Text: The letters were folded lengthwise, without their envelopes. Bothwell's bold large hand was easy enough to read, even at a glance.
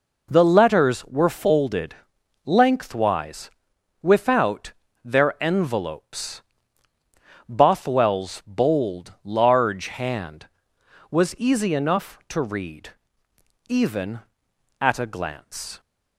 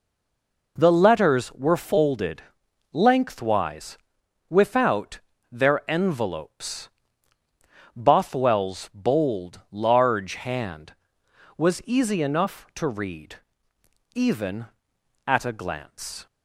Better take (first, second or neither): first